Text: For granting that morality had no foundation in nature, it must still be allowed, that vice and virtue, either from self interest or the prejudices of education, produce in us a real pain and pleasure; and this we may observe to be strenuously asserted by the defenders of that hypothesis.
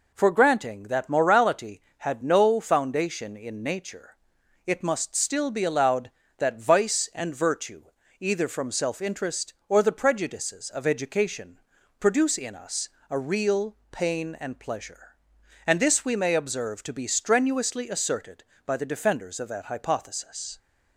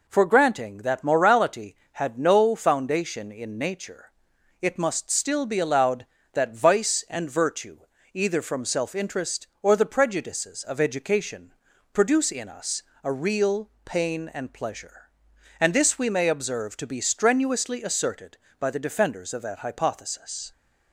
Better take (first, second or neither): neither